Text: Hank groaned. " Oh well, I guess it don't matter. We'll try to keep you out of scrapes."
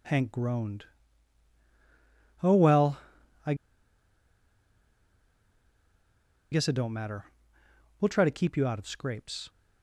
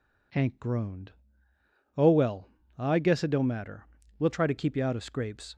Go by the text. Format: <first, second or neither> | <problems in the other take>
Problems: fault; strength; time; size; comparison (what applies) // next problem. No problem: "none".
second | pauses between "I" and "guess"; strong; at 3.5 s; 2.9 s long